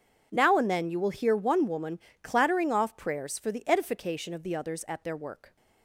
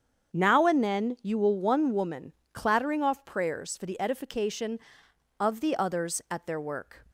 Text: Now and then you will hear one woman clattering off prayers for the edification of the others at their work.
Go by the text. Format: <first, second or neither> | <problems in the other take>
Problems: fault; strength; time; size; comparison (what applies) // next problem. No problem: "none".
first | starts louder than the rest; strong; until 1.4 s; 7.5 dB // skips "hear"; at 1.5 s // pauses between "woman" and "clattering"; slight; at 2.3 s; 0.20 s long; slight in the first